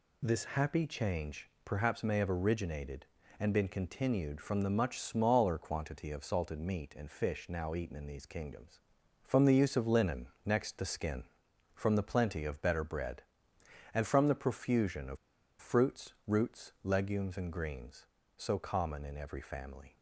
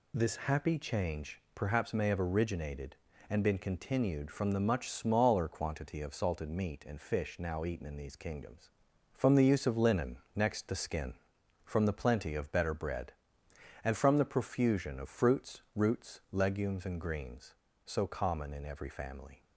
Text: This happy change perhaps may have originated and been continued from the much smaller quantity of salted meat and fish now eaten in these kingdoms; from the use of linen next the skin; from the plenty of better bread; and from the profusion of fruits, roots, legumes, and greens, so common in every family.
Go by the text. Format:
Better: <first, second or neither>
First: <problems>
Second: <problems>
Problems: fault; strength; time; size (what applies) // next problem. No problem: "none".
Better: second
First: pauses between "change" and "perhaps"; slight; at 1.4 s; 0.16 s long // pauses between "linen" and "next"; slight; at 10.2 s; 0.16 s long // pauses between "of" and "fruits"; at 15.1 s; 0.44 s long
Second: pauses between "linen" and "next"; slight; at 10.1 s; 0.16 s long